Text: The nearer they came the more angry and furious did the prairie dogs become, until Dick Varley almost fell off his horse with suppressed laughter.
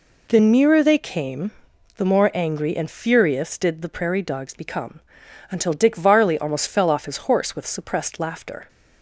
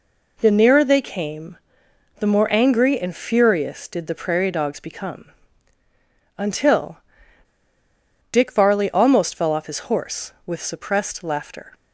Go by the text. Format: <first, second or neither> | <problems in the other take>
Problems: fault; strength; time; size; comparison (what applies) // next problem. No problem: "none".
first | pauses between "came" and "the"; noticeable; at 1.5 s; 0.64 s long; noticeable in the first // pauses between "until" and "Dick"; strong; at 6.9 s; 1.3 s long